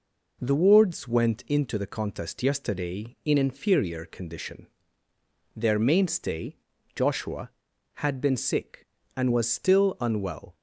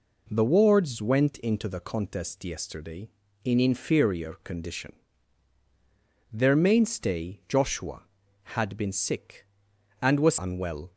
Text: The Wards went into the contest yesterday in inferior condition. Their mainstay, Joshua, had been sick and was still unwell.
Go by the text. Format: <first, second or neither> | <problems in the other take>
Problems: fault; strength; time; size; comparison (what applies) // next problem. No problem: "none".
first | skips "still"; at 10.3 s